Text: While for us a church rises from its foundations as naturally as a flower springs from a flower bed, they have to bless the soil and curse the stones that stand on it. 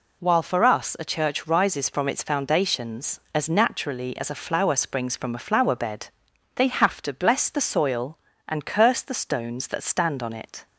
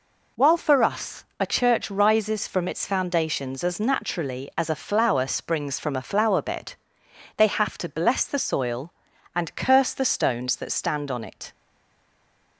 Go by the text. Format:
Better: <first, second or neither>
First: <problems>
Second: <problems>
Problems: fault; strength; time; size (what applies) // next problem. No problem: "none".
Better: first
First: none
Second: pauses between "us" and "a"; slight; at 1.2 s; 0.16 s long // stays silent after the last word; from 11.5 s on; 1.0 s long